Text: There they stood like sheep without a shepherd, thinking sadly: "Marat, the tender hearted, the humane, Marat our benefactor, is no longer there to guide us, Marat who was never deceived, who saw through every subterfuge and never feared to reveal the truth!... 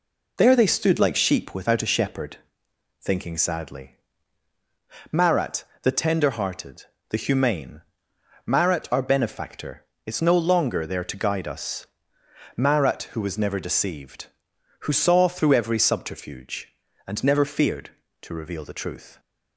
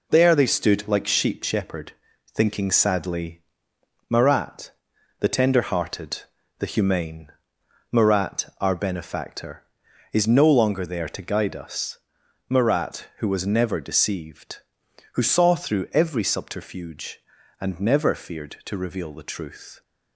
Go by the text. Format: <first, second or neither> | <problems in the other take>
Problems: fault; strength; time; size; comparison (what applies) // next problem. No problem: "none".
first | skips "without a"; at 1.4 s